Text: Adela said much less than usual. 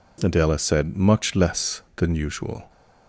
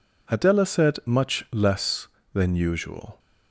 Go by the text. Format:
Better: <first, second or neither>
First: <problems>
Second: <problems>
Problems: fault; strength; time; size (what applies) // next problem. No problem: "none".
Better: neither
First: none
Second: none